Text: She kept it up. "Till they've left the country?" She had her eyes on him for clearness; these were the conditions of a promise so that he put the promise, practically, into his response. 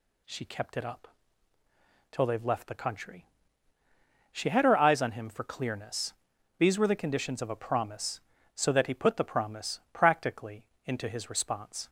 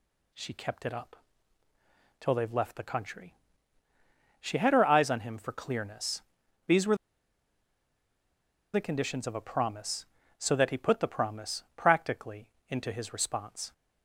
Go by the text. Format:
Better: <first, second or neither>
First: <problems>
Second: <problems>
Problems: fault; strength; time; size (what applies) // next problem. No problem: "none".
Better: first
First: none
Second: pauses between "were" and "the"; strong; at 6.9 s; 1.7 s long